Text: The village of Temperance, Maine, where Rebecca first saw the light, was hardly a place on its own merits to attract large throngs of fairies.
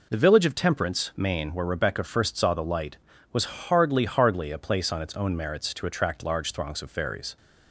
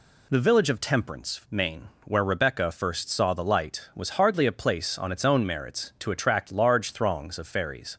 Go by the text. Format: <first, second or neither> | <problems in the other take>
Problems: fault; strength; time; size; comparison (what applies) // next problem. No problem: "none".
second | says "hardly" twice; at 4.0 s